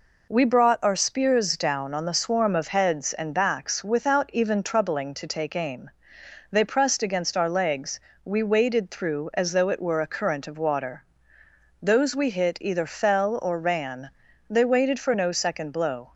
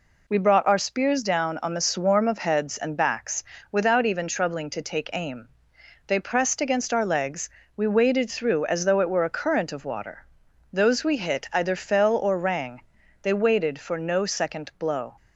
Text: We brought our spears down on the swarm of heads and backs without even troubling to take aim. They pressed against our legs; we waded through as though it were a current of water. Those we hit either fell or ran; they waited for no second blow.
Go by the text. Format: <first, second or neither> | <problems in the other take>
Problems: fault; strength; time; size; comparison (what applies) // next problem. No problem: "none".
first | pauses between "backs" and "without"; slight; at 3.4 s; 0.30 s long // says "rang" for "ran"; at 12.3 s